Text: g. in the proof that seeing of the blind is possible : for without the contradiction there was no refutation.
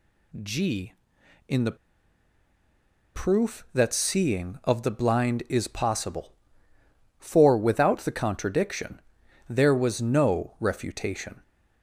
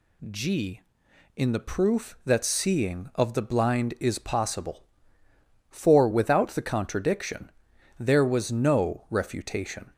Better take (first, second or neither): second